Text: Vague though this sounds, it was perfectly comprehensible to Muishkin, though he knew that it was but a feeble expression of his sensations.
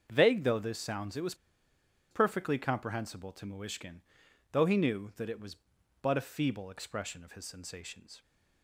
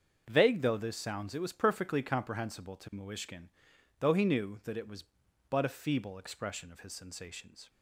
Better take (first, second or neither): second